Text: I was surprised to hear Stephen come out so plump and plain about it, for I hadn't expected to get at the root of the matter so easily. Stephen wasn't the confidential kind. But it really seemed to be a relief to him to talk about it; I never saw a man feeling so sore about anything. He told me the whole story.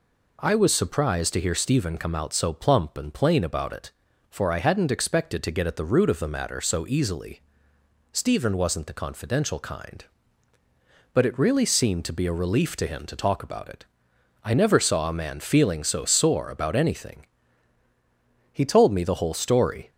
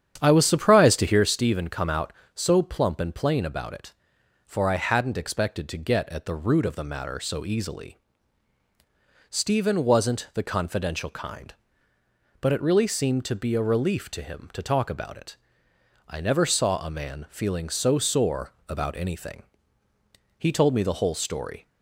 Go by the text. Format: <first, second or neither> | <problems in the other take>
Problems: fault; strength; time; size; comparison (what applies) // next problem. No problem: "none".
first | starts louder than the rest; strong; until 1.2 s; 9 dB // pauses between "sore" and "about"; slight; at 18.5 s; 0.16 s long